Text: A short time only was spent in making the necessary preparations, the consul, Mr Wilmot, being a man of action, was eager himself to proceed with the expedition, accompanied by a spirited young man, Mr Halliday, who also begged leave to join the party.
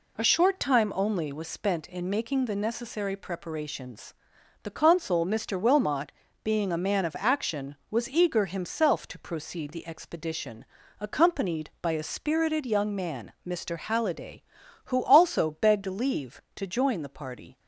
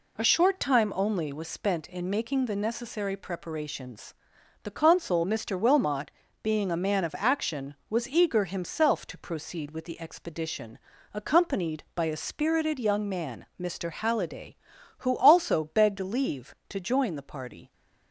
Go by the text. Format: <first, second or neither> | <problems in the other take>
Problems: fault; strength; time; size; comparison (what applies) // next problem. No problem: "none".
second | skips "with"; at 9.7 s